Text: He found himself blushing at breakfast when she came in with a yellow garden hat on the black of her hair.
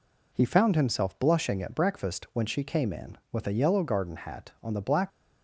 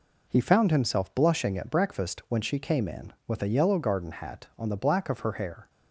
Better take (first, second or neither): second